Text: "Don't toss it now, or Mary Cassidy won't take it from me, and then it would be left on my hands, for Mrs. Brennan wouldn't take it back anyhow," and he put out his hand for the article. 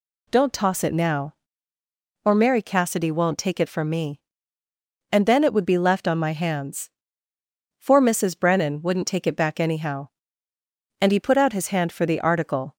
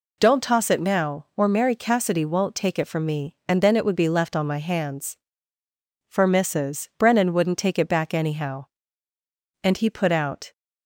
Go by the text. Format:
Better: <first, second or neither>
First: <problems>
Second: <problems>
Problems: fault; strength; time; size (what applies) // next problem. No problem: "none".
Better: first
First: none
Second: stops before "his hand for the article"; at 10.5 s